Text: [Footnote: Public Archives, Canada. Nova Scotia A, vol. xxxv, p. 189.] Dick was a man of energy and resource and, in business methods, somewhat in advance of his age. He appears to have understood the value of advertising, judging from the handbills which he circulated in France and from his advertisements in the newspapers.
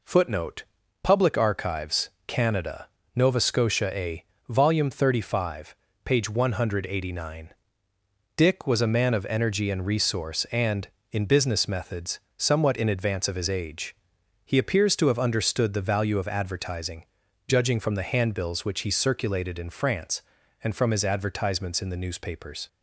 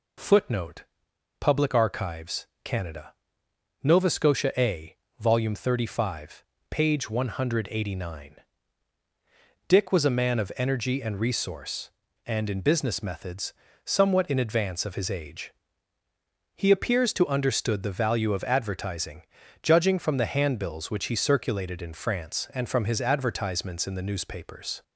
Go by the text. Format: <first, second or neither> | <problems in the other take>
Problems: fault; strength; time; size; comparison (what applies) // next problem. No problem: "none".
first | skips "have"; at 17.2 s